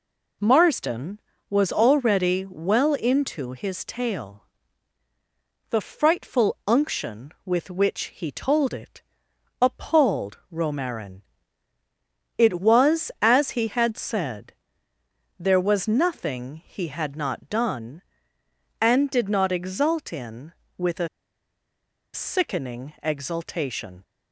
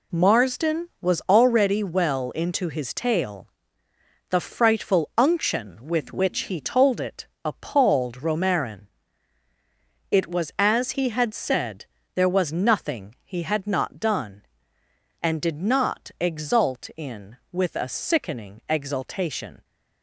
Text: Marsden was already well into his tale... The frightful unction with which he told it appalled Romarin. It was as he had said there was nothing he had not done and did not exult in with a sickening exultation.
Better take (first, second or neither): second